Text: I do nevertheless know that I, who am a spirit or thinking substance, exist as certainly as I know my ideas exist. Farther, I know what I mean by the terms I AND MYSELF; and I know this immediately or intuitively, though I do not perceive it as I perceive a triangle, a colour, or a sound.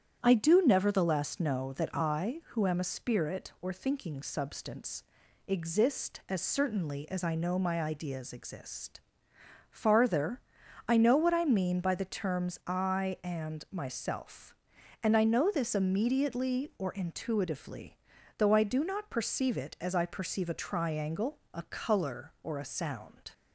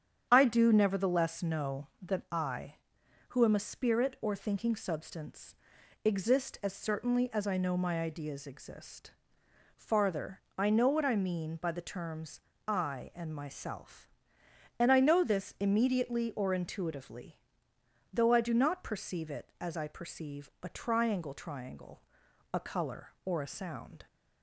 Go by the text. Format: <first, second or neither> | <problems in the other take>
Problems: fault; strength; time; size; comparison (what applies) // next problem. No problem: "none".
first | starts louder than the rest; strong; until 1.3 s; 8.5 dB; strong in the first // pauses between "terms" and "I"; slight; at 12.4 s; 0.26 s long // says "triangle" twice; at 21.3 s